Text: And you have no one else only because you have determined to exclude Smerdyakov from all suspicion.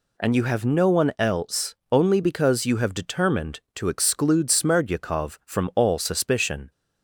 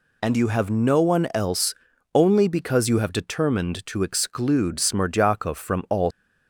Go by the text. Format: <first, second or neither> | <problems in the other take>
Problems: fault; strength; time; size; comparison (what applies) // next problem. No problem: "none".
first | pauses between "else" and "only"; at 1.7 s; 0.40 s long; slight in the first // stops before "suspicion"; at 6.0 s